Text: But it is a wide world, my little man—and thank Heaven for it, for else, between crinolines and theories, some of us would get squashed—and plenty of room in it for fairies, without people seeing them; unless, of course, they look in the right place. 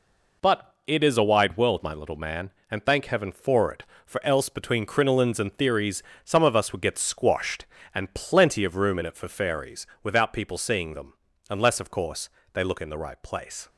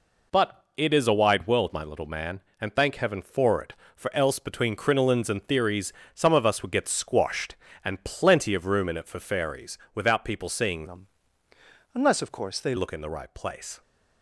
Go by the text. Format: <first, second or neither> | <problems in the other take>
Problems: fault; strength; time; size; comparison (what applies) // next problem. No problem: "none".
first | changes voice from "them" to "they"; from 10.8 to 12.7 s; 1.9 s long